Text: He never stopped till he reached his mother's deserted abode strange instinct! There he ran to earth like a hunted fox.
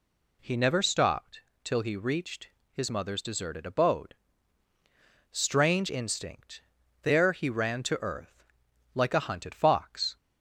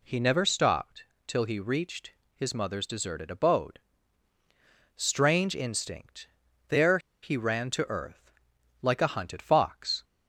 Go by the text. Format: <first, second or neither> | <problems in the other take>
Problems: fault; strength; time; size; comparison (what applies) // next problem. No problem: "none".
first | pauses between "stopped" and "till"; slight; at 1.0 s; 0.22 s long; slight in the first // pauses between "reached" and "his"; slight; at 2.1 s; 0.22 s long; slight in the first // pauses between "abode" and "strange"; at 3.7 s; 1.1 s long; also in the first // pauses between "There" and "he"; slight; at 6.9 s; 0.24 s long // pauses between "earth" and "like"; noticeable; at 8.3 s; 0.50 s long; noticeable in the first